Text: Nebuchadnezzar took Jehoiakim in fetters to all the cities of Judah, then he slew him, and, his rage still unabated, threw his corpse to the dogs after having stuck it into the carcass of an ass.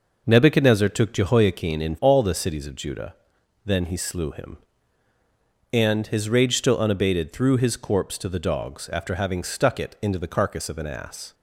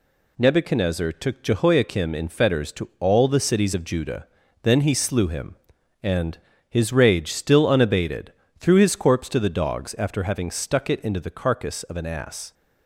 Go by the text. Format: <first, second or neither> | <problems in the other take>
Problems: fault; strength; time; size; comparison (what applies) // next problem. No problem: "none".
second | skips "fetters to"; at 1.9 s